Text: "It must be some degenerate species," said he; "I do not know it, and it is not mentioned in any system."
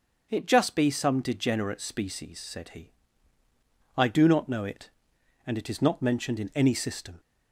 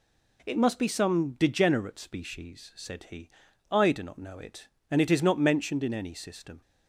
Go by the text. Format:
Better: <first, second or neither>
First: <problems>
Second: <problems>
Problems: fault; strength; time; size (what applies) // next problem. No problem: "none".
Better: second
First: starts louder than the rest; until 1.3 s; 6 dB // says "just" for "must"; at 0.4 s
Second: none